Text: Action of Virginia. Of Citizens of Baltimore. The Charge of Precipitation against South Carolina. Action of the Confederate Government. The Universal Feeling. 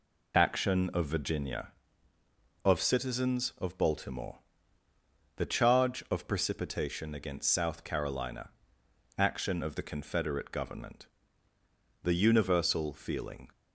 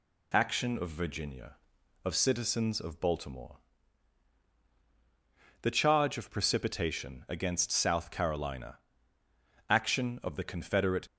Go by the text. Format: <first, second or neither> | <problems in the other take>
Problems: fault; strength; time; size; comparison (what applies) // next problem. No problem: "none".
first | stops before "Government The Universal Feeling"; at 11.0 s